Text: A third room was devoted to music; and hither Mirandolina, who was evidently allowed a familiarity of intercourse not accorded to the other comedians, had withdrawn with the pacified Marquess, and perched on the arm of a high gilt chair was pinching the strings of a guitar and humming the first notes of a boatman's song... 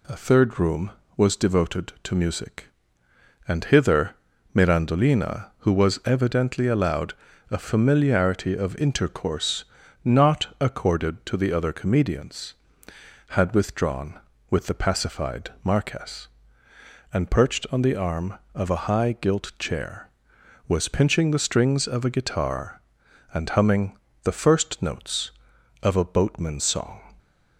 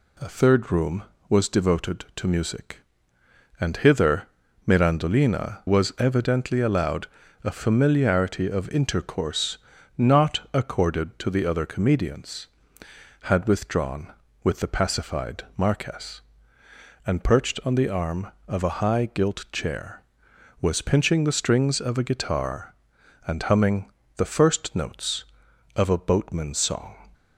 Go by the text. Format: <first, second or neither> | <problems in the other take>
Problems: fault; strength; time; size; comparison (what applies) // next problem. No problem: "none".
first | pauses between "hither" and "Mirandolina"; at 4.2 s; 0.40 s long; also in the first // skips "who"; at 5.6 s // pauses between "allowed" and "a"; slight; at 7.0 s; 0.36 s long; slight in the first // pauses between "intercourse" and "not"; at 9.5 s; 0.40 s long; also in the first // pauses between "humming" and "the"; slight; at 23.9 s; 0.24 s long; slight in the first